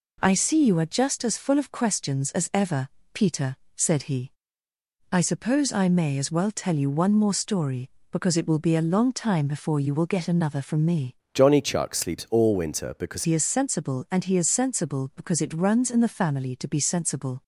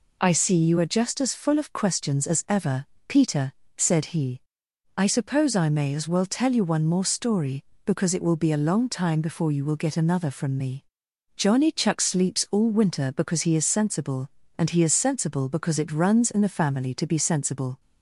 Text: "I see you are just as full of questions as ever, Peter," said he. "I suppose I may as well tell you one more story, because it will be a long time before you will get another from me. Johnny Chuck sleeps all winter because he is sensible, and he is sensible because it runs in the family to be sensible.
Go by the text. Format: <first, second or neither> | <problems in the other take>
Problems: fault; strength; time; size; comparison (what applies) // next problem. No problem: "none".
second | changes voice from "Johnny" to "because"; from 11.3 to 13.2 s; 1.9 s long